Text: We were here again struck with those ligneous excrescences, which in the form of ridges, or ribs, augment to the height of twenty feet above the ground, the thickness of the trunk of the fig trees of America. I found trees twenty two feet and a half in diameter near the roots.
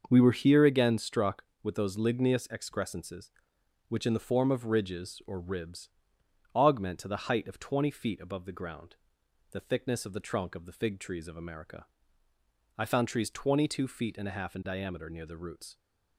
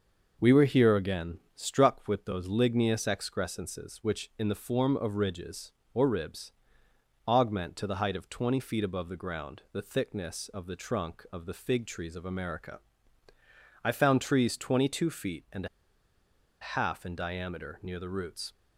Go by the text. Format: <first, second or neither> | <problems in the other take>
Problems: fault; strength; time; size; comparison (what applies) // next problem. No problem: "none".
first | starts louder than the rest; noticeable; until 1.5 s; 6 dB; also in the first // pauses between "and" and "a"; noticeable; at 15.6 s; 0.95 s long